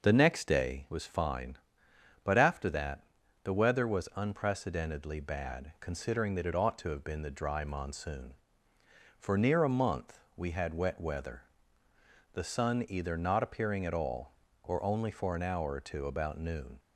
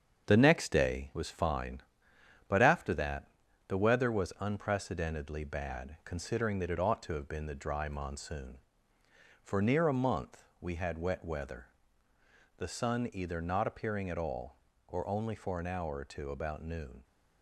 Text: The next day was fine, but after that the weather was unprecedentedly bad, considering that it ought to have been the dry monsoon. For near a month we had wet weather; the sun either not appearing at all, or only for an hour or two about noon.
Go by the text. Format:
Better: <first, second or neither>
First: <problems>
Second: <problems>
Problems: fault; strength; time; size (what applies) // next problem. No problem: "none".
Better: first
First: pauses between "that" and "the"; at 3.0 s; 0.40 s long // pauses between "month" and "we"; slight; at 10.2 s; 0.16 s long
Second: gets quieter; noticeable; throughout; 5.5 dB // pauses between "that" and "the"; at 3.2 s; 0.40 s long // pauses between "month" and "we"; slight; at 10.4 s; 0.16 s long